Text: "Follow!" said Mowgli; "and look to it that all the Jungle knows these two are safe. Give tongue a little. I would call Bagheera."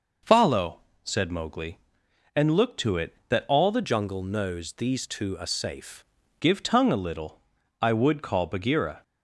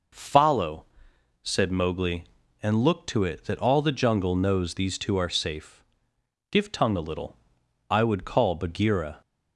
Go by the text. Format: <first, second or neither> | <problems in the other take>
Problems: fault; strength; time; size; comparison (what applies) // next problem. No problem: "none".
second | changes voice from "Jungle" to "safe"; from 3.8 to 6.0 s; 2.2 s long